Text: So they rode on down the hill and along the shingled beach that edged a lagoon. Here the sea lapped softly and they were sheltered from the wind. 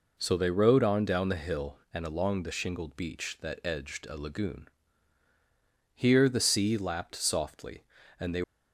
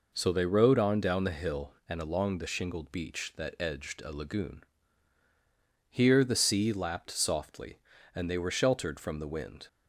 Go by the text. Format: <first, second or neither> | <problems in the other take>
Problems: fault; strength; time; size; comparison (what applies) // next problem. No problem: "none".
second | stops before "were sheltered from the wind"; at 8.4 s